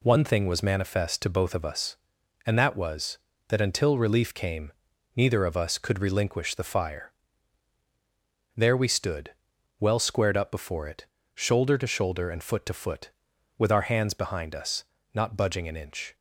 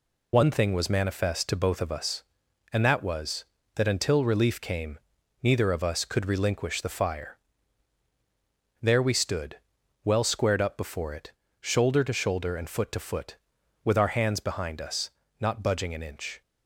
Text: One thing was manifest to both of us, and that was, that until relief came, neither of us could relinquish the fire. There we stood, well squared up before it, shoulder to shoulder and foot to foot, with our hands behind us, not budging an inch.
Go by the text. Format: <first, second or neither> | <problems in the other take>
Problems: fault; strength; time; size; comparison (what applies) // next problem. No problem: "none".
first | loses the start of "One"; at 0.3 s; 50 ms